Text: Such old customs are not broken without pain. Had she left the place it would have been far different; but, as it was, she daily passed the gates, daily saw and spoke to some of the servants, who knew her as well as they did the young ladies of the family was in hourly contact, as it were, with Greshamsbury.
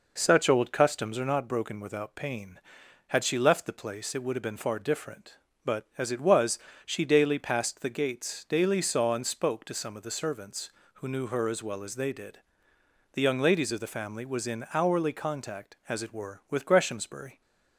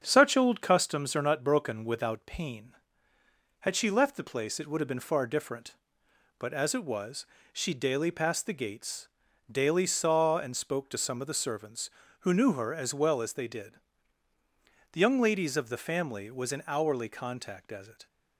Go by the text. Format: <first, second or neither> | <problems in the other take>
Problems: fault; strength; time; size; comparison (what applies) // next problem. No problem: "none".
first | starts louder than the rest; strong; until 1.0 s; 7 dB // pauses between "did" and "the"; at 13.7 s; 1.1 s long; noticeable in the first // stops before "were with Greshamsbury"; at 18.0 s